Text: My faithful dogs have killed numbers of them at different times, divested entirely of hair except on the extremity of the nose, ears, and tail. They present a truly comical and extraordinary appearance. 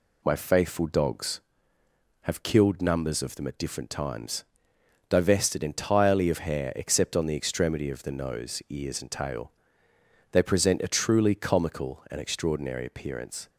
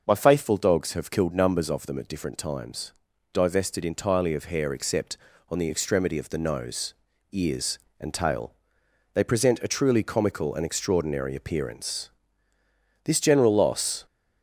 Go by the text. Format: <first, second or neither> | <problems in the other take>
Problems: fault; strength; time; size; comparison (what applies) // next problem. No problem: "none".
first | goes on to say "This general loss"; noticeable; from 13.0 s on; 1.0 s long